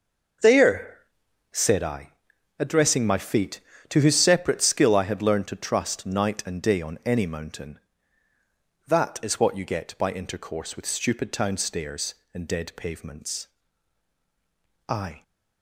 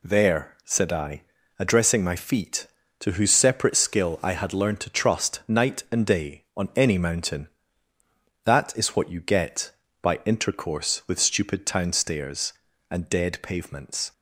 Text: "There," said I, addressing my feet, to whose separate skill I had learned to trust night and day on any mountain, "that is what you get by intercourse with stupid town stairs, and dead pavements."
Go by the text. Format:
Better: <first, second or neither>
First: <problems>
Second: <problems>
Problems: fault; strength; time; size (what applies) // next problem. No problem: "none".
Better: second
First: starts louder than the rest; until 1.9 s; 6.5 dB // goes on to say "I"; slight; from 14.9 s on; 0.32 s long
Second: none